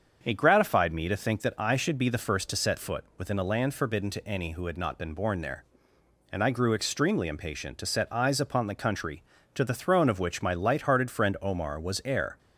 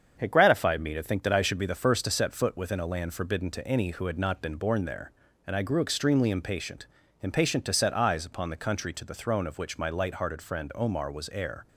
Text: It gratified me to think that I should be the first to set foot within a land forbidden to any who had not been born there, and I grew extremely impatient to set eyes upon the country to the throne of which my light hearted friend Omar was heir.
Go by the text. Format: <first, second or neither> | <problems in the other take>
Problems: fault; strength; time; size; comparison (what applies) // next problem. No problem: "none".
first | starts louder than the rest; strong; until 1.2 s; 7.5 dB; also in the first // says "impatient" twice; at 7.2 s